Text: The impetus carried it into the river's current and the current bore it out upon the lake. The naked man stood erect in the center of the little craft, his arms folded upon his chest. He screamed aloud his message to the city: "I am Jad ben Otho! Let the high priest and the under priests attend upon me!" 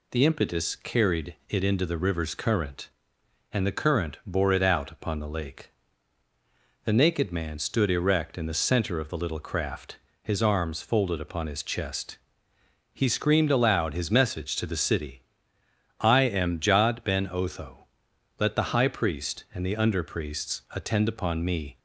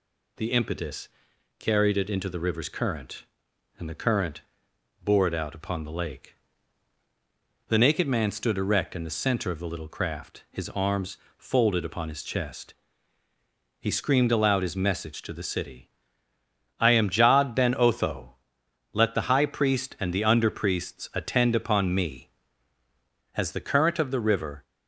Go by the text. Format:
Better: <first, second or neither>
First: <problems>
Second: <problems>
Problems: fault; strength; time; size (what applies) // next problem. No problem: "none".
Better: first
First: none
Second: pauses between "impetus" and "carried"; noticeable; at 1.0 s; 0.50 s long // pauses between "current" and "bore"; noticeable; at 4.4 s; 0.62 s long // pauses between "arms" and "folded"; slight; at 11.1 s; 0.20 s long // goes on to say "As the current of the river"; noticeable; from 23.3 s on; 1.2 s long